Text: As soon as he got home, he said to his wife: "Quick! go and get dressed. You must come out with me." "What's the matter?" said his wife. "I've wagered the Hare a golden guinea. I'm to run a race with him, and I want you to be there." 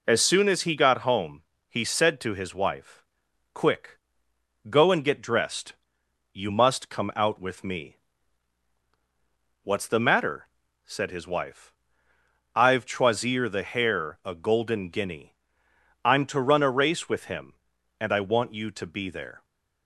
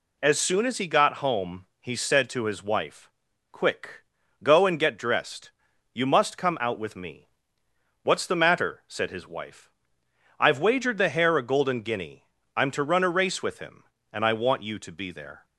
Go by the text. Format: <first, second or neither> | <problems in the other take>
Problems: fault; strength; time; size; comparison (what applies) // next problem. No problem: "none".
second | says "choisir" for "wagered"; at 12.8 s